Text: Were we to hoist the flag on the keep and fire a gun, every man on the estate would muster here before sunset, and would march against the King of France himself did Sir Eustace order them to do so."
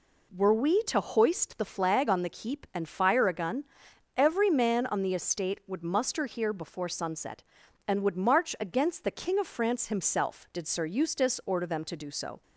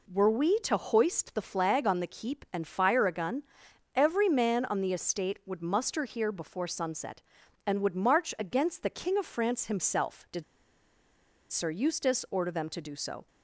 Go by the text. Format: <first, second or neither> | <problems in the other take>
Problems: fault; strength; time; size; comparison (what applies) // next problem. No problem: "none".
first | pauses between "did" and "Sir"; at 10.4 s; 1.0 s long